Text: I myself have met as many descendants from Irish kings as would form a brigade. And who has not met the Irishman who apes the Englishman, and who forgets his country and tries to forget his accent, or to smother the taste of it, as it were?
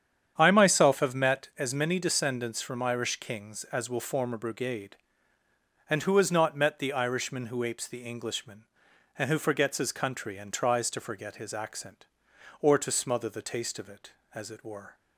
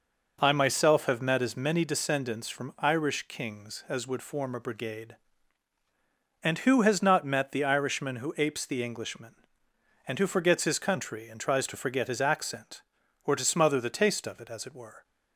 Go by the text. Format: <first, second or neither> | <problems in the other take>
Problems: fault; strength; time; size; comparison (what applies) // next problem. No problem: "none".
second | starts louder than the rest; strong; until 1.3 s; 8.5 dB // says "will" for "would"; at 3.8 s